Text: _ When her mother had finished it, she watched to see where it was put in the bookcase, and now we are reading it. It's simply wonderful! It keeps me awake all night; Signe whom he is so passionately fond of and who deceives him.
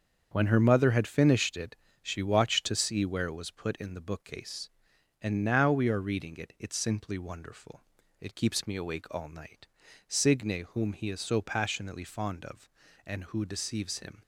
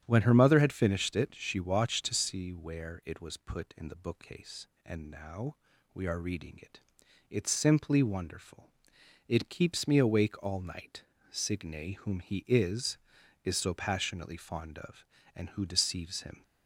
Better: first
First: starts louder than the rest; until 1.3 s; 7 dB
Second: starts louder than the rest; strong; until 1.0 s; 9.5 dB // pauses between "now" and "we"; at 5.5 s; 0.40 s long // says "is" twice; at 13.4 s

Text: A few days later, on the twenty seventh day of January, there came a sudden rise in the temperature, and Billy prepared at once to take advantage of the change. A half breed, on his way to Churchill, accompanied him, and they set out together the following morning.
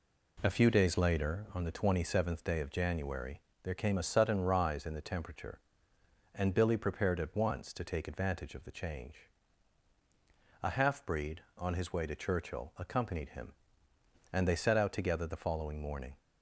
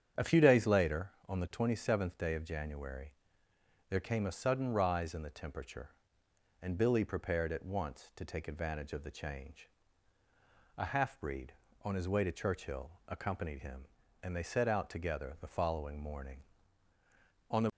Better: first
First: none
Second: starts louder than the rest; strong; until 1.3 s; 8.5 dB // goes on to say "On the"; slight; from 17.5 s on; 0.18 s long

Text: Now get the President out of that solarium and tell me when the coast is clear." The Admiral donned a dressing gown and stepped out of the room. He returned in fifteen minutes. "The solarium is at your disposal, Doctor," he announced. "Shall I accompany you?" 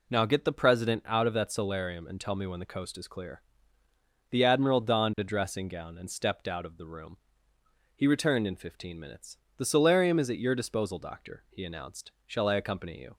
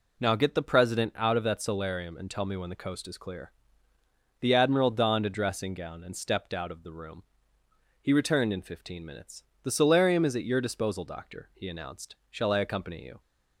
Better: neither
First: none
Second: none

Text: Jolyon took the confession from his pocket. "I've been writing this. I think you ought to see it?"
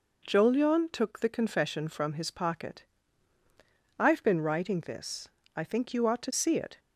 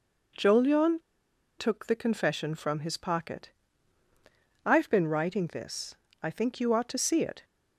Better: first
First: none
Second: pauses between "Jolyon" and "took"; noticeable; at 0.9 s; 0.59 s long

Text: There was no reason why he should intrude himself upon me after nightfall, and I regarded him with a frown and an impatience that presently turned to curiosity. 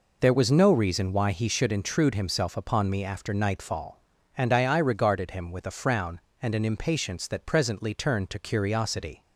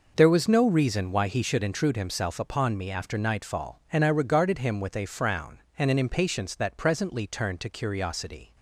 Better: second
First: says "I" twice; at 4.6 s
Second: none

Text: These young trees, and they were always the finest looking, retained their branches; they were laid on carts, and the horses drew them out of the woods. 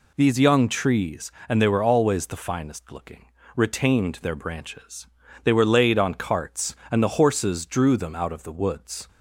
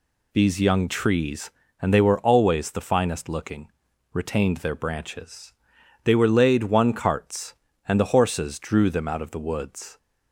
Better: first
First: none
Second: says "one" for "on"; at 6.6 s

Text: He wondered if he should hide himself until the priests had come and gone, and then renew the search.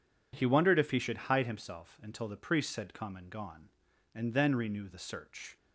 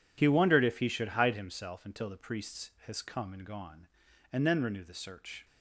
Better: first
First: none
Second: says "has" for "had"; at 2.8 s

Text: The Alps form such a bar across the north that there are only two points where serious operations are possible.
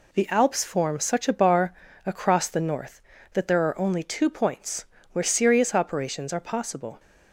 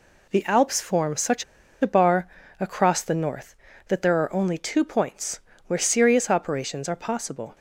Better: first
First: pauses between "bar" and "across"; slight; at 1.7 s; 0.32 s long // pauses between "points" and "where"; slight; at 4.8 s; 0.28 s long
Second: pauses between "such" and "a"; at 1.4 s; 0.39 s long // pauses between "bar" and "across"; slight; at 2.2 s; 0.32 s long // pauses between "points" and "where"; slight; at 5.3 s; 0.28 s long

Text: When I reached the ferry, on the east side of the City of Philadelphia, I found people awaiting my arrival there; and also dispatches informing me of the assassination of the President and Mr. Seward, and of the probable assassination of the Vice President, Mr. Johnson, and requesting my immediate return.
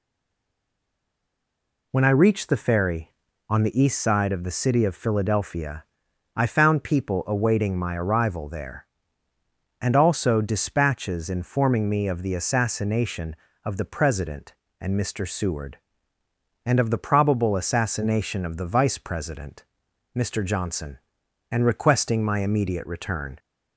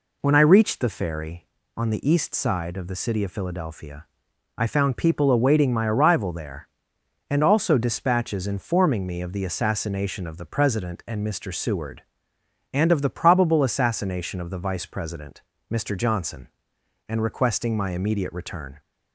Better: second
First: stays silent before the first word; noticeable; until 1.9 s; 1.9 s long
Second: none

